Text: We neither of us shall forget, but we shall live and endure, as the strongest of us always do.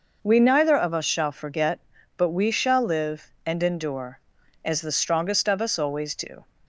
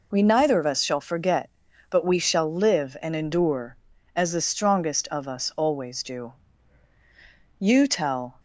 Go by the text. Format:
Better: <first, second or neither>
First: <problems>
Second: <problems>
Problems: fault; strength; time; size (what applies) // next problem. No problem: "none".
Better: first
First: none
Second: goes on to say "You tell"; noticeable; from 7.5 s on; 0.80 s long